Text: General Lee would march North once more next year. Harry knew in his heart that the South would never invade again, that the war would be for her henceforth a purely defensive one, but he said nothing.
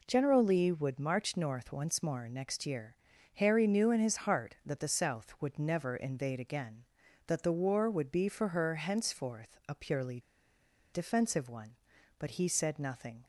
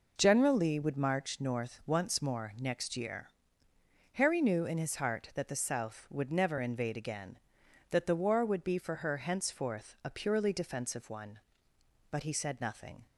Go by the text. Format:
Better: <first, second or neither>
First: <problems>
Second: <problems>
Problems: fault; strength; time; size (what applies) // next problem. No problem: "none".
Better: second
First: pauses between "purely" and "defensive"; noticeable; at 10.1 s; 0.72 s long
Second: none